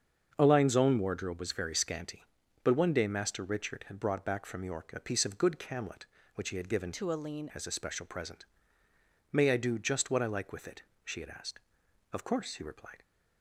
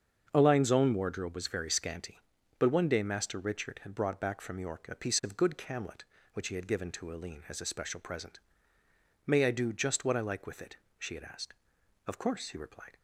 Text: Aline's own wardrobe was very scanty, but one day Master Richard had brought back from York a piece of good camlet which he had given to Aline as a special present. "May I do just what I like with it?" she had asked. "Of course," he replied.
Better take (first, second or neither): second